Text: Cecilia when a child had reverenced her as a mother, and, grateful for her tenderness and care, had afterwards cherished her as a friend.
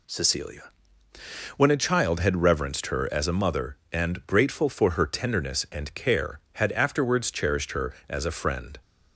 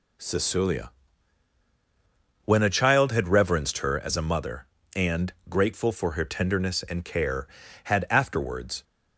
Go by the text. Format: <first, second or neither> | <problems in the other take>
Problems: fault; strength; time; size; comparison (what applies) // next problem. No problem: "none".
first | pauses between "Cecilia" and "when"; strong; at 0.9 s; 1.5 s long; noticeable in the first // stops before "cherished her as a friend"; at 8.8 s